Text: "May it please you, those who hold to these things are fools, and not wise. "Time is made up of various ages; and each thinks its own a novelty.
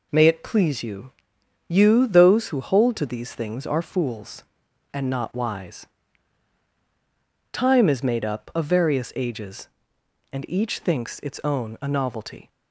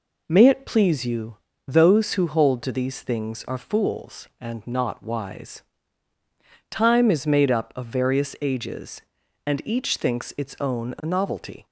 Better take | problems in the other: second | says "you" twice; at 1.6 s

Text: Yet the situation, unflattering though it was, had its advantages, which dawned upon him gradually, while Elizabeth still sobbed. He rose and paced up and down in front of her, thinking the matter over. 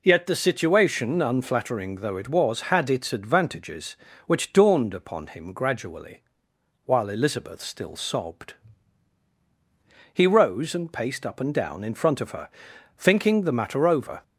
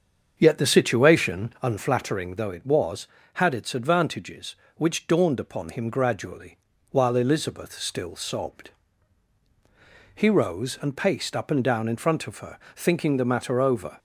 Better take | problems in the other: first | starts louder than the rest; strong; until 1.6 s; 7 dB

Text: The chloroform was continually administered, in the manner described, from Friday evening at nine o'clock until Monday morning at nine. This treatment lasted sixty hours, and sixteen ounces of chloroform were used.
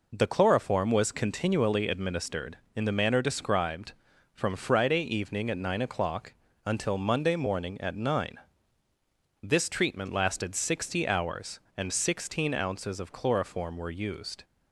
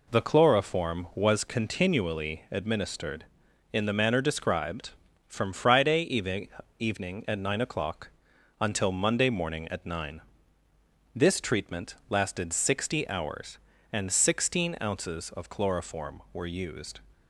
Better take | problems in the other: first | says "evening" twice; at 6.7 s // pauses between "o'clock" and "until"; noticeable; at 8.0 s; 0.50 s long; slight in the first

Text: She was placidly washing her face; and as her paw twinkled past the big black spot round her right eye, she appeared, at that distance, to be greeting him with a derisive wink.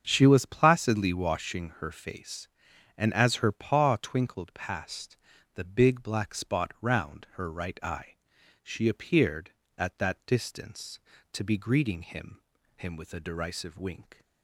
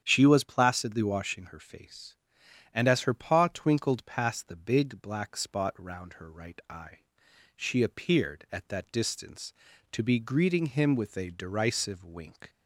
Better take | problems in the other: second | starts louder than the rest; strong; until 1.0 s; 7 dB; strong in the second // pauses between "past" and "the"; at 5.1 s; 0.40 s long // says "him" twice; at 12.7 s

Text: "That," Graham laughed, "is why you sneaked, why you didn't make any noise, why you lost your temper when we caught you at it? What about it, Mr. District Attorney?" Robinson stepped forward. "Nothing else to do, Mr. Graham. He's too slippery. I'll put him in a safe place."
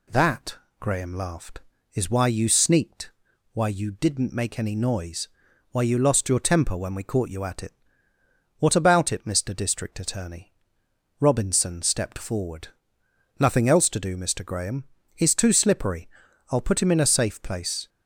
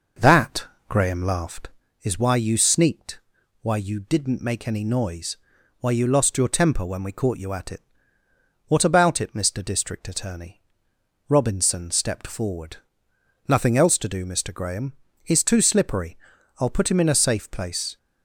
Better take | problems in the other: first | starts louder than the rest; noticeable; until 1.8 s; 5.5 dB

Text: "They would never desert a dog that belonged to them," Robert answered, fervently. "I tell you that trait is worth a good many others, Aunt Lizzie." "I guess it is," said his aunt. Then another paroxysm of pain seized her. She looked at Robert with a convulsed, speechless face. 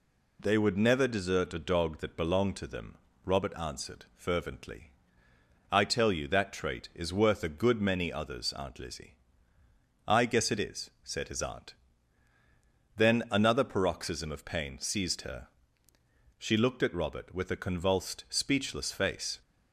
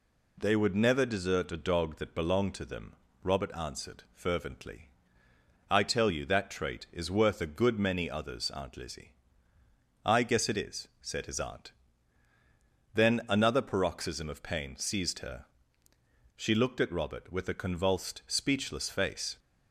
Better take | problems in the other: neither | none

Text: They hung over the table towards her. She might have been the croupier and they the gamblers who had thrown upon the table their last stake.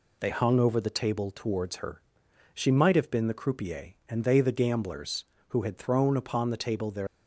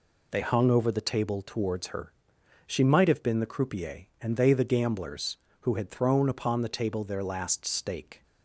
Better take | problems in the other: second | stops before "last stake"; at 7.0 s

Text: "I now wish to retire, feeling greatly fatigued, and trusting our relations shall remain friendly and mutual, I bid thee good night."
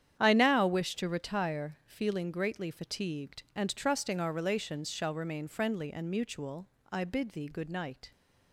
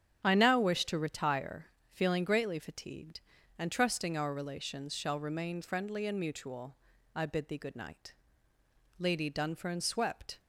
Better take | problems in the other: first | starts louder than the rest; strong; until 1.2 s; 9 dB; strong in the first // goes on to say "Lady Dunfern swept"; from 8.9 s on; 1.4 s long

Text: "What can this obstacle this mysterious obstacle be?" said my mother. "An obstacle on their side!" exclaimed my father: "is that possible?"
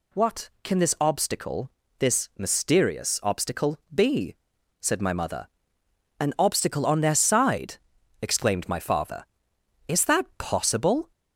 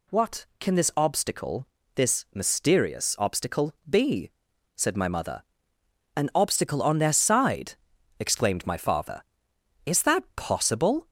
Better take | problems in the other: neither | pauses between "obstacle" and "this"; slight; the same in both // pauses between "obstacle" and "be"; slight; the same in both

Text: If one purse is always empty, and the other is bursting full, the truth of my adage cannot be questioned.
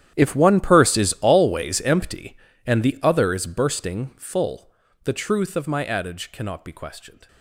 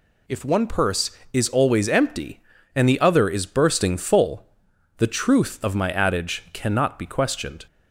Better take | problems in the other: second | gets quieter; strong; throughout; 18.5 dB

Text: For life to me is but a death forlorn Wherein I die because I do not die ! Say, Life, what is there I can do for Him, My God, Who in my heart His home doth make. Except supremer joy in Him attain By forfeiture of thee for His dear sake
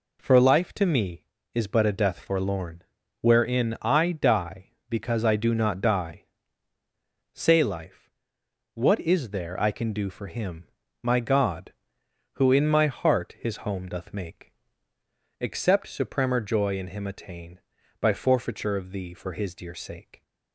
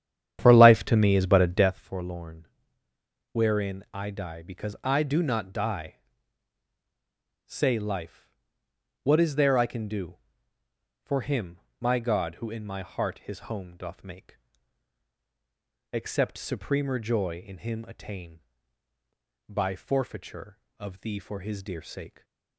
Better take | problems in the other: first | starts louder than the rest; strong; until 1.7 s; 10 dB // pauses between "forlorn" and "Wherein"; noticeable; at 2.4 s; 0.86 s long; also in the first

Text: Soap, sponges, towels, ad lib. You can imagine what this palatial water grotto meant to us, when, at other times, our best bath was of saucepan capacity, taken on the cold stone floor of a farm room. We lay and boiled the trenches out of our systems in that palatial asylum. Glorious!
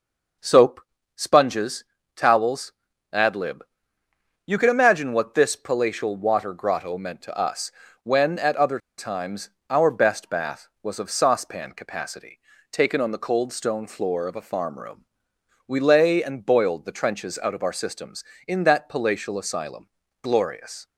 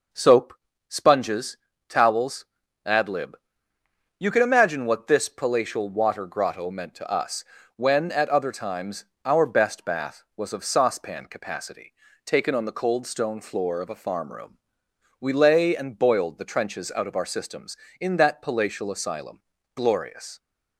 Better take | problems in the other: second | pauses between "other" and "times"; slight; at 8.7 s; 0.19 s long

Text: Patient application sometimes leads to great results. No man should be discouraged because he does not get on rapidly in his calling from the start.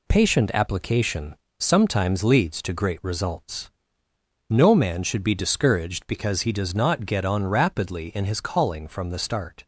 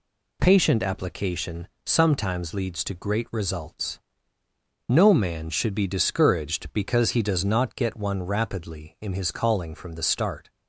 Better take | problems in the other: first | pauses between "application" and "sometimes"; slight; at 1.6 s; 0.18 s long; slight in the first // says "one" for "on"; at 7.9 s

